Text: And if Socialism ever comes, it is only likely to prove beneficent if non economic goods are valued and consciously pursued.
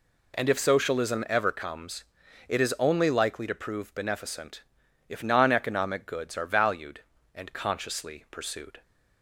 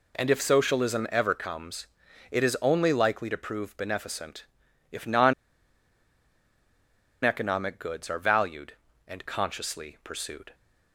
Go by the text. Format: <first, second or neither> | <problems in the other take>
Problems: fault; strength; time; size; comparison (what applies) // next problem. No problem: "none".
first | pauses between "beneficent" and "if"; at 4.4 s; 0.44 s long; also in the first // pauses between "non" and "economic"; strong; at 5.3 s; 1.9 s long